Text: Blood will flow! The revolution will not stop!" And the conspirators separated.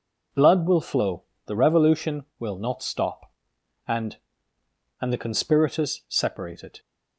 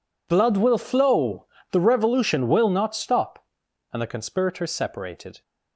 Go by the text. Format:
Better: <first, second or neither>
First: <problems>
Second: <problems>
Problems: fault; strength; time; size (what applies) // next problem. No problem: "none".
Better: second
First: says "And" twice; at 5.0 s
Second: none